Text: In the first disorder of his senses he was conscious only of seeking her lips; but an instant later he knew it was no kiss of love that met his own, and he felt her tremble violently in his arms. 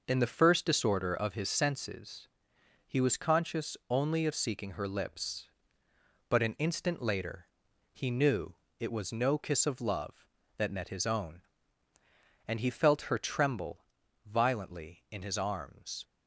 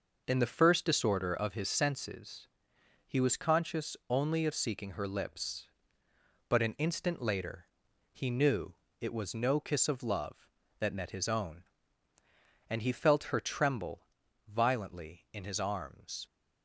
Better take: neither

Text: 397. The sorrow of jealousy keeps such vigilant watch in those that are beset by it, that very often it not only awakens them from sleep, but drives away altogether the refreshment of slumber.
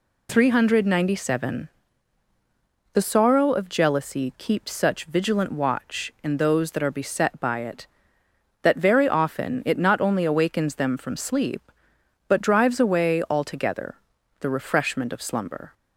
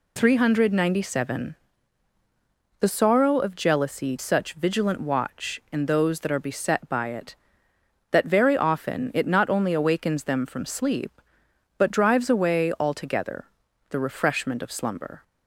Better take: first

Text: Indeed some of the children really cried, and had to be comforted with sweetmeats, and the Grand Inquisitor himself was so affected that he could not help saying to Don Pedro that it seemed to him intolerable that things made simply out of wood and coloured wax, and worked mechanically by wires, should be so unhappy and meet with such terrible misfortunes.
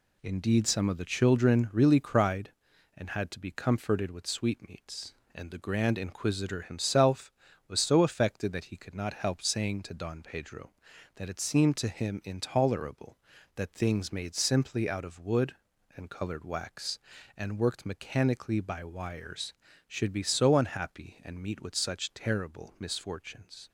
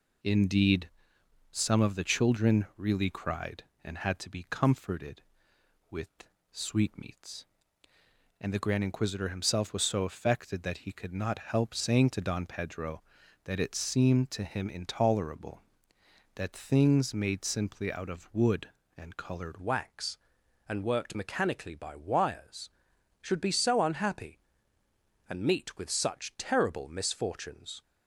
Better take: first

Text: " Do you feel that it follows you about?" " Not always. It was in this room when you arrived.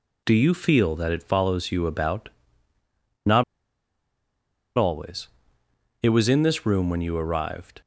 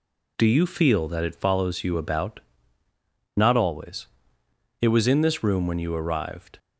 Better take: second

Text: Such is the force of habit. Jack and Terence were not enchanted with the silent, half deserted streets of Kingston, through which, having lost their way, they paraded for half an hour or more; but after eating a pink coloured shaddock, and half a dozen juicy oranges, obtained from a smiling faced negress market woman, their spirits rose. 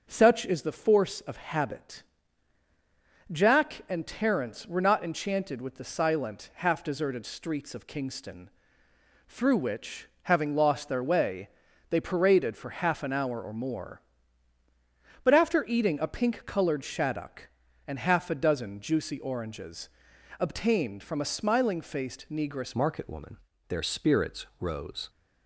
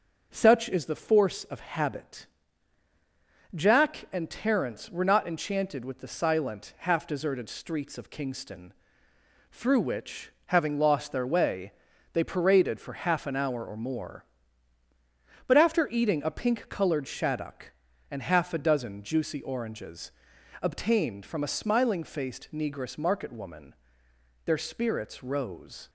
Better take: second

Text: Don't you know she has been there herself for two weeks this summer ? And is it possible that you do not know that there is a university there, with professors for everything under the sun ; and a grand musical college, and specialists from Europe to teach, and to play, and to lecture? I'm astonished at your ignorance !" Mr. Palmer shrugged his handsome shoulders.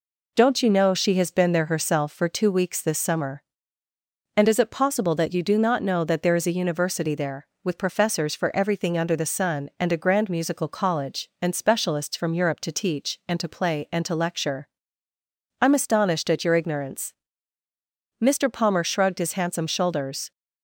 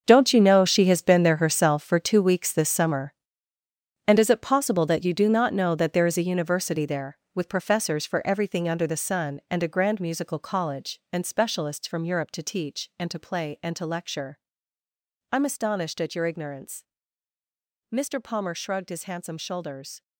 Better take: first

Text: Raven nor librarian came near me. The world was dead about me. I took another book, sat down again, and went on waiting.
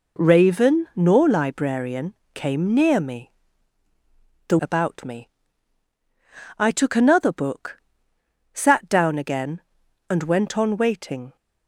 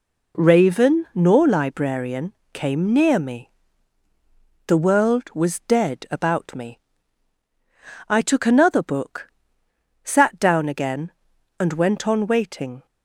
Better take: second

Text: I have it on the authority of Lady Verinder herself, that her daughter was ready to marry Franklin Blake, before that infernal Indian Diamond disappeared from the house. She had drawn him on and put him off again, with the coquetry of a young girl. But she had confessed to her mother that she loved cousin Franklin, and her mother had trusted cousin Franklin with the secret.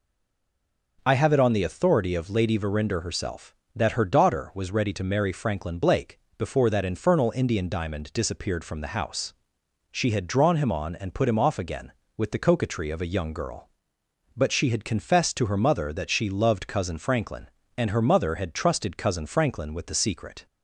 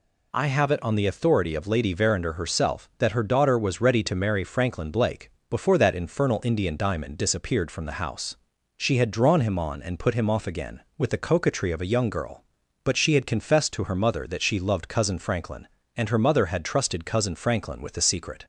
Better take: second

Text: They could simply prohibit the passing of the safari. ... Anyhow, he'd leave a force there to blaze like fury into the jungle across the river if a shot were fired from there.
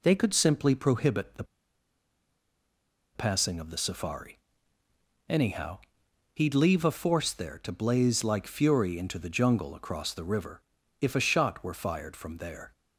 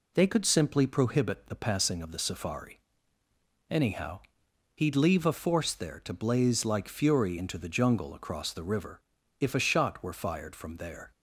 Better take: second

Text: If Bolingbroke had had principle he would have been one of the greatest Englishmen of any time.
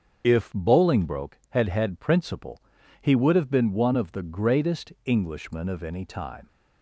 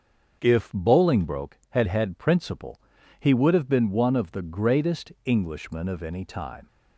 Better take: second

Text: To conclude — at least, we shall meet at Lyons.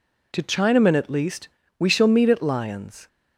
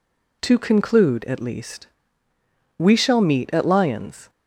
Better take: second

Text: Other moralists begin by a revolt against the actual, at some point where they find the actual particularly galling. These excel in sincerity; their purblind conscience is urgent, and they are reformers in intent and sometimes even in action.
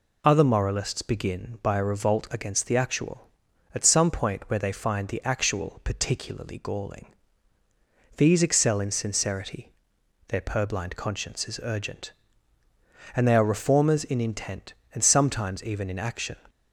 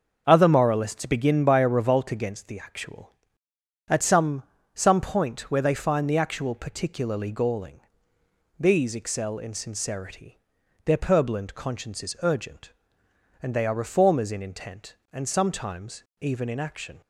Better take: first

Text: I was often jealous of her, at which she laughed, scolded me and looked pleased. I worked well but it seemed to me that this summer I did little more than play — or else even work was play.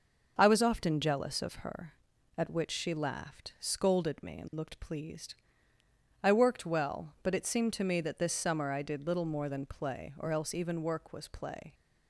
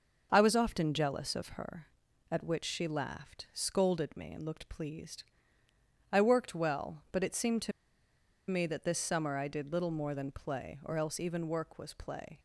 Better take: first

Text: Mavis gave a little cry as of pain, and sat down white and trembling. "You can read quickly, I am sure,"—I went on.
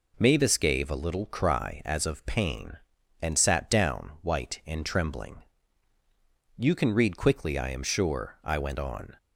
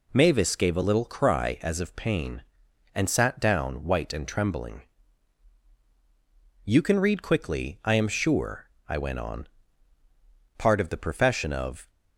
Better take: first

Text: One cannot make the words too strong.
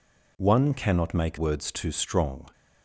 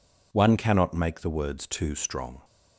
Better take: second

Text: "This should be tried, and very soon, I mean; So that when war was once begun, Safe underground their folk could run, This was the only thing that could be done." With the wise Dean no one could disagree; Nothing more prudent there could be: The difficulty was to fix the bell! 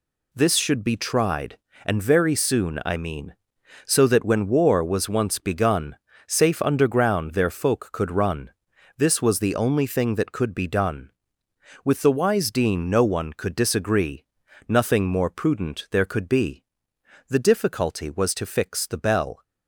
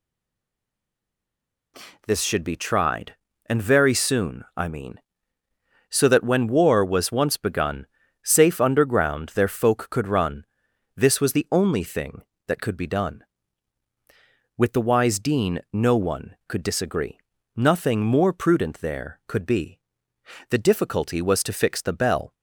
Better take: first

